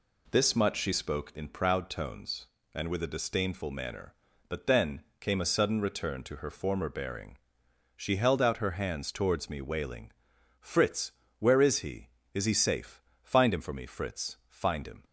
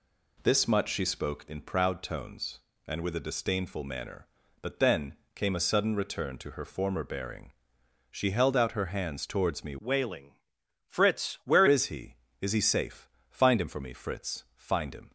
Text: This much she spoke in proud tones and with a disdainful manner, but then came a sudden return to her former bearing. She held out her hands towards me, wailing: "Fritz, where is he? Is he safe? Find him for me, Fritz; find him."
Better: first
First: pauses between "then" and "came"; slight; at 5.0 s; 0.18 s long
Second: pauses between "then" and "came"; slight; at 5.1 s; 0.20 s long // changes voice from "wailing" to "where"; from 9.7 to 11.6 s; 1.9 s long

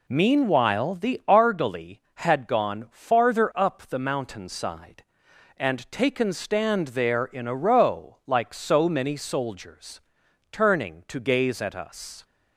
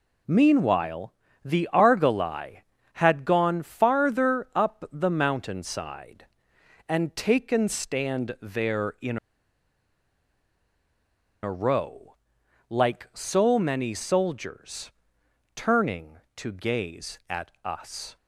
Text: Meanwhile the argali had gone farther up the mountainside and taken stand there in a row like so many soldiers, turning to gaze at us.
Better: first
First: none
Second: pauses between "Meanwhile" and "the"; slight; at 1.1 s; 0.32 s long // pauses between "in" and "a"; strong; at 9.1 s; 2.2 s long // pauses between "row" and "like"; noticeable; at 12.1 s; 0.52 s long

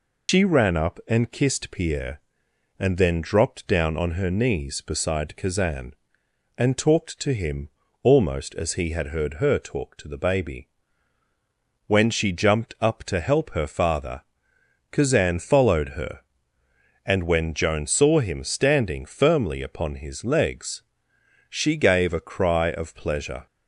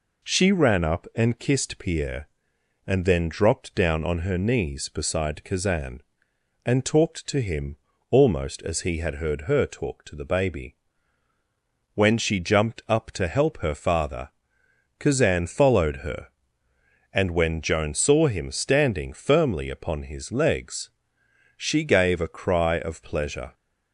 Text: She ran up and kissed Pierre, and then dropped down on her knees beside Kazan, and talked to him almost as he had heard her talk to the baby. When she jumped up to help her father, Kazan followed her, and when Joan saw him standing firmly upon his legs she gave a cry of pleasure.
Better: second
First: loses the start of "She"; at 0.2 s; 135 ms // pauses between "him" and "almost"; slight; at 7.6 s; 0.34 s long // pauses between "legs" and "she"; noticeable; at 20.8 s; 0.66 s long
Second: pauses between "him" and "almost"; slight; at 7.7 s; 0.34 s long // pauses between "legs" and "she"; noticeable; at 20.8 s; 0.66 s long

